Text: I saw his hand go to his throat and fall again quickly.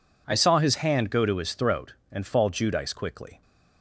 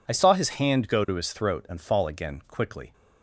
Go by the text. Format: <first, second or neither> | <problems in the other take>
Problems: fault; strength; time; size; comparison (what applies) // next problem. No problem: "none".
second | says "judice" for "again"; at 2.4 s